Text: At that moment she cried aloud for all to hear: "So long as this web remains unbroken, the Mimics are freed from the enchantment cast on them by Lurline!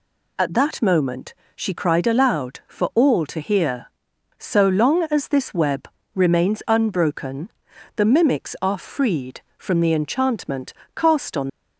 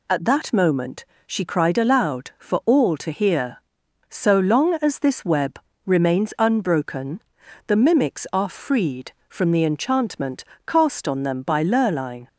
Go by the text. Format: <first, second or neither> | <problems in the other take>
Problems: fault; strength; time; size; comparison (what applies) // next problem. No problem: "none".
second | pauses between "moment" and "she"; slight; at 1.3 s; 0.22 s long; slight in the second // pauses between "web" and "remains"; slight; at 5.8 s; 0.26 s long; slight in the second // pauses between "enchantment" and "cast"; slight; at 10.7 s; 0.20 s long; slight in the second // stops before "them by Lurline"; at 11.4 s